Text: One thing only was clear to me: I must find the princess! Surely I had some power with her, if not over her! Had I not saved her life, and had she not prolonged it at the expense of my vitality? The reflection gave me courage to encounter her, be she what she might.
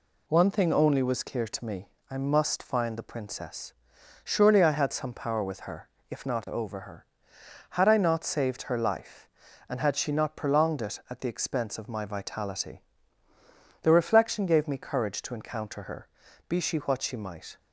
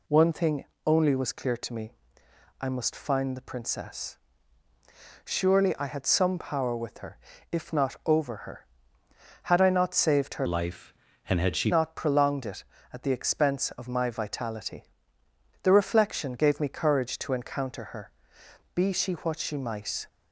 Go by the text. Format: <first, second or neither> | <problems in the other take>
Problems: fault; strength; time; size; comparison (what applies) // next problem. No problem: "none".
first | pauses between "thing" and "only"; slight; at 0.6 s; 0.20 s long // changes voice from "life" to "she"; from 10.4 to 11.7 s; 1.3 s long